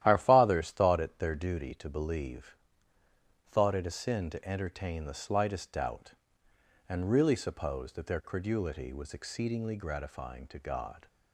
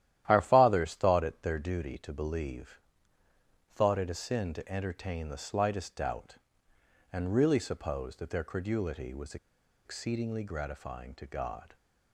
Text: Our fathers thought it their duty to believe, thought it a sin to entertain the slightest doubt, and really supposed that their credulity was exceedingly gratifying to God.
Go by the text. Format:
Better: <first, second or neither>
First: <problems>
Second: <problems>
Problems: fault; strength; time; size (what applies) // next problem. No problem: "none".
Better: first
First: starts louder than the rest; strong; until 1.0 s; 12.5 dB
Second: starts louder than the rest; strong; until 1.2 s; 12.5 dB // pauses between "was" and "exceedingly"; noticeable; at 9.3 s; 0.49 s long